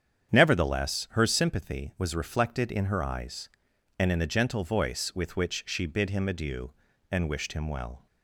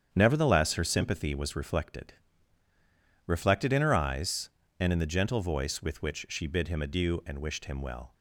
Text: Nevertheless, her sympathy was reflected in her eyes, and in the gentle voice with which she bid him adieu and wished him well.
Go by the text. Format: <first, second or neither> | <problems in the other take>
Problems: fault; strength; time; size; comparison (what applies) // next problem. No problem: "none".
first | starts louder than the rest; strong; until 1.1 s; 8 dB; strong in the first // says "reflected" twice; at 3.2 s